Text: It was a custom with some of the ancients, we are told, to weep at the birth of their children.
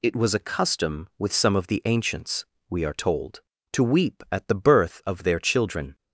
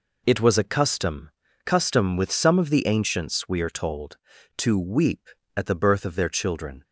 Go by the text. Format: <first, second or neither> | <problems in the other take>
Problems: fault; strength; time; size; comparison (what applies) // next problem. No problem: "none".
first | says "custom" twice; at 1.6 s